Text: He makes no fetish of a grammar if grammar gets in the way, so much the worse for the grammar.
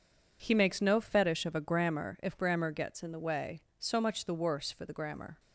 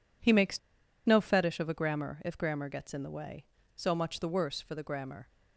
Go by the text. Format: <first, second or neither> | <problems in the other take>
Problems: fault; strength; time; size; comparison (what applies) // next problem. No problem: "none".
first | pauses between "makes" and "no"; noticeable; at 0.5 s; 0.46 s long